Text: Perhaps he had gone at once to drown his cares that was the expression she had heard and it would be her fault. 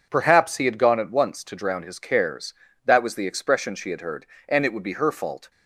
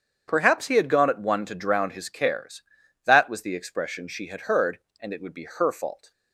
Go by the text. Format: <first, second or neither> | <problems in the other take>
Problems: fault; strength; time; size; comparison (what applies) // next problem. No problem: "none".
first | starts louder than the rest; strong; until 1.2 s; 7.5 dB // says "one" for "once"; at 1.1 s